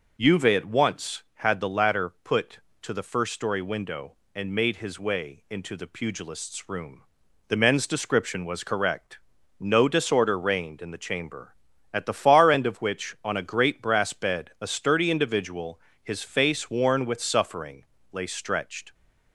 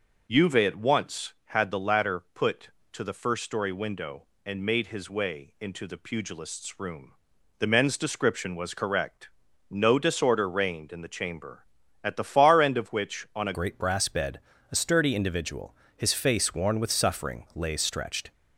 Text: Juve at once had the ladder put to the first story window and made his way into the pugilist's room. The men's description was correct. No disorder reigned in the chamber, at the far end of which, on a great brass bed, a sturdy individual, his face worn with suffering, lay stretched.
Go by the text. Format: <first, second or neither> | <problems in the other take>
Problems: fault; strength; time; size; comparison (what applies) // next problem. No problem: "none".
first | changes voice at "great"; from 13.5 s on; 4.8 s long